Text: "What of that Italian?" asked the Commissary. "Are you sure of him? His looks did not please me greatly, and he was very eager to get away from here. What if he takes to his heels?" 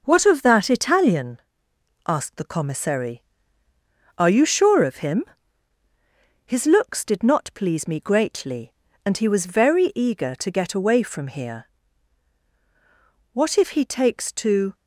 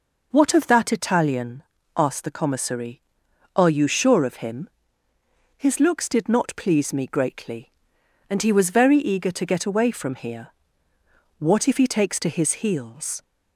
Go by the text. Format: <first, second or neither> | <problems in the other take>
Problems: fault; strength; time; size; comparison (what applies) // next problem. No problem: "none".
second | stops before "his heels"; at 14.7 s